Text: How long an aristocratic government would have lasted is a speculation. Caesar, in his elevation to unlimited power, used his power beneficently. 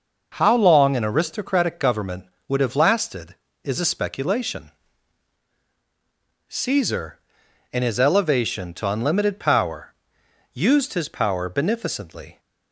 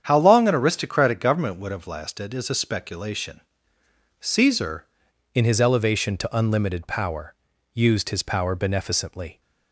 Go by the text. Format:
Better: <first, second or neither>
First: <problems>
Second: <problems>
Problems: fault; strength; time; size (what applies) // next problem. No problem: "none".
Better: first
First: none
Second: starts louder than the rest; strong; until 1.0 s; 8.5 dB // changes voice at "in"; from 5.3 s on; 4.1 s long